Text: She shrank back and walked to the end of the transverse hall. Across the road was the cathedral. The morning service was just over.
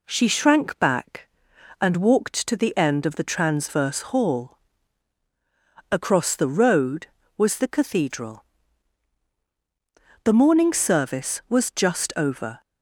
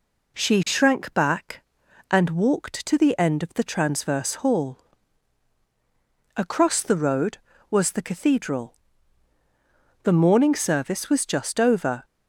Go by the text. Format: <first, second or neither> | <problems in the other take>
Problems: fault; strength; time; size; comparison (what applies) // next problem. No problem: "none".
neither | none